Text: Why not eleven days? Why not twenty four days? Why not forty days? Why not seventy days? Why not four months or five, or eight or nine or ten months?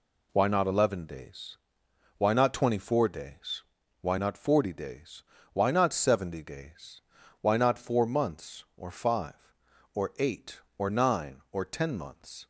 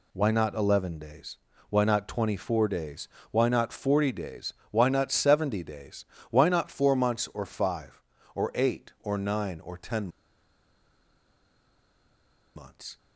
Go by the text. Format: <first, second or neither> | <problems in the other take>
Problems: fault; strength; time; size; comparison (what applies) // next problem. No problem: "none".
first | pauses between "ten" and "months"; strong; at 10.0 s; 2.4 s long